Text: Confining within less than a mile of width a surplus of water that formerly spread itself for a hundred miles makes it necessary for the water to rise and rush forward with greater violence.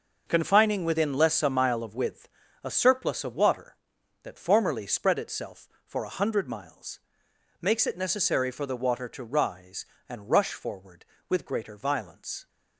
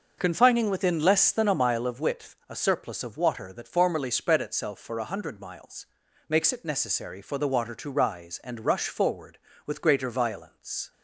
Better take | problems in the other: second | starts louder than the rest; noticeable; until 1.2 s; 6 dB // skips "than"; at 1.4 s // pauses between "width" and "a"; slight; at 2.2 s; 0.34 s long // pauses between "miles" and "makes"; noticeable; at 6.9 s; 0.62 s long; also in the second

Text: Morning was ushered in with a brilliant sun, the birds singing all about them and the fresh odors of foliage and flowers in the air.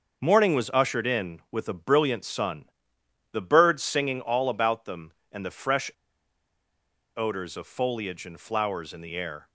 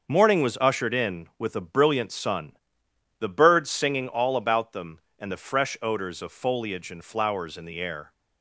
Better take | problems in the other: second | starts louder than the rest; until 1.2 s; 6.5 dB; also in the second // pauses between "fresh" and "odors"; strong; at 5.8 s; 1.2 s long

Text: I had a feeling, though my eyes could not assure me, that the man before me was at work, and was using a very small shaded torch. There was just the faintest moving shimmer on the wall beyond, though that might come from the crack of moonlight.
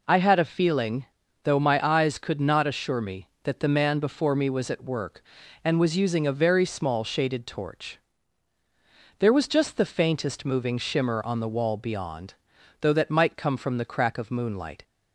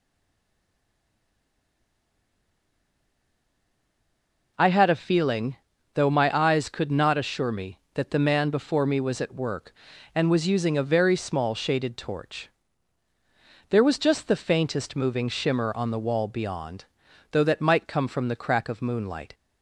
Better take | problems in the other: first | stays silent before the first word; strong; until 4.5 s; 4.5 s long

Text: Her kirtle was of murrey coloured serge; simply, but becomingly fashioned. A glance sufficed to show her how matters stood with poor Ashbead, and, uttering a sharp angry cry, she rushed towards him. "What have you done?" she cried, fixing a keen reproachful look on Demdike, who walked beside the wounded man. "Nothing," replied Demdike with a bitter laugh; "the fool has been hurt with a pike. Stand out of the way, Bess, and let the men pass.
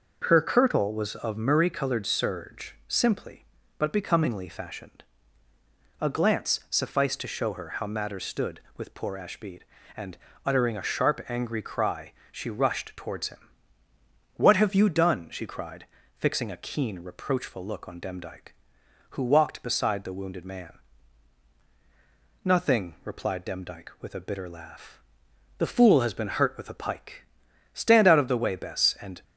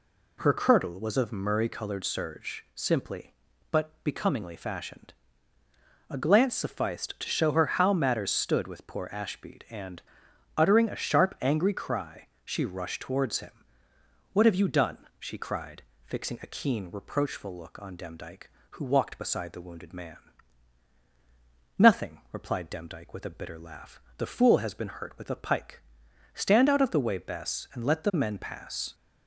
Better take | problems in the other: second | stops before "let the men pass"; at 29.2 s

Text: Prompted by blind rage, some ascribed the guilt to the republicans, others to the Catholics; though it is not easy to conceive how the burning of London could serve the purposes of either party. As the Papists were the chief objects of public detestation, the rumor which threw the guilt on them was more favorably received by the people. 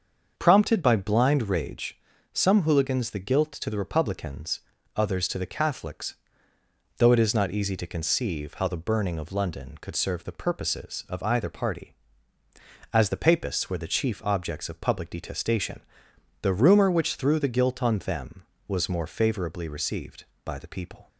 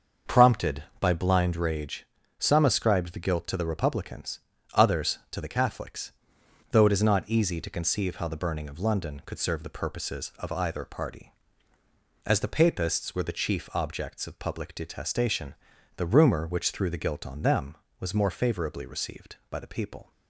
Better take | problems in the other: second | starts louder than the rest; until 1.3 s; 7 dB; also in the second // says "hooligans" for "ascribed"; at 2.6 s

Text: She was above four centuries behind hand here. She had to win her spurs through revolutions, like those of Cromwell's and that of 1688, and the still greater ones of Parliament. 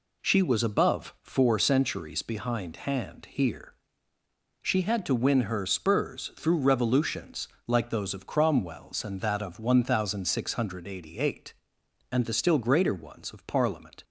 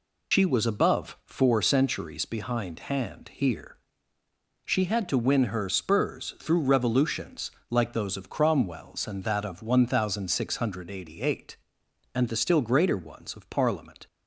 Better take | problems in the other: first | loses the start of "She"; at 0.3 s; 70 ms

